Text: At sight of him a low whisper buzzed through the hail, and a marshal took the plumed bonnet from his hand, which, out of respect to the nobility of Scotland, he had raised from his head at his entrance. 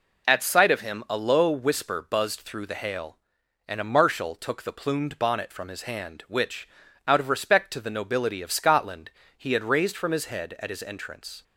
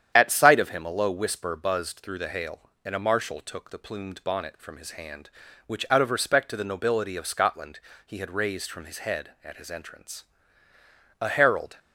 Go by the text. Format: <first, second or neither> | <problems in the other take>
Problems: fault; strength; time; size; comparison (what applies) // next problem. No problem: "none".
first | starts louder than the rest; strong; until 1.1 s; 9 dB // goes on to say "A herald"; from 11.2 s on; 0.58 s long